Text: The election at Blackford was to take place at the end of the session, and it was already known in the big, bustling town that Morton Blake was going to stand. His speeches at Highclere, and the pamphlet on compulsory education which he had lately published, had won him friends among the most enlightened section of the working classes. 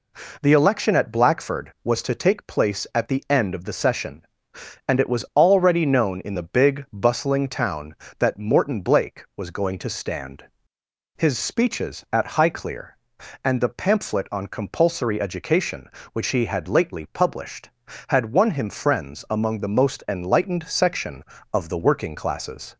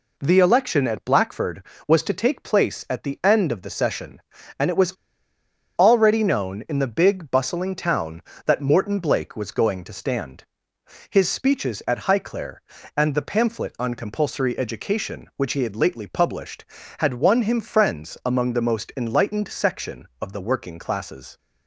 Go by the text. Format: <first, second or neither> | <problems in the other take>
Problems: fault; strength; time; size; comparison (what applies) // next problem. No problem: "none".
first | pauses between "was" and "already"; noticeable; at 4.9 s; 0.83 s long